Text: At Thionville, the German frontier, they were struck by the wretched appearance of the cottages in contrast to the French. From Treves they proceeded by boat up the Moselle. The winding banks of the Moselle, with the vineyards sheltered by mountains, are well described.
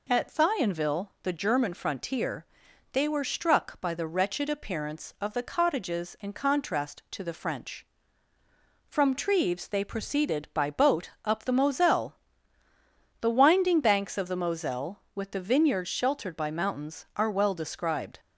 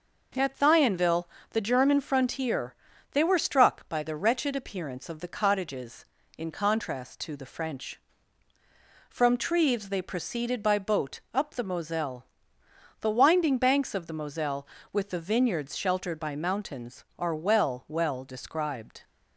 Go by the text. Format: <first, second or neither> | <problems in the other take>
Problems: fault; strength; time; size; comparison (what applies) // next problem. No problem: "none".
first | pauses between "boat" and "up"; slight; at 11.1 s; 0.16 s long; slight in the first // says "well" twice; at 17.8 s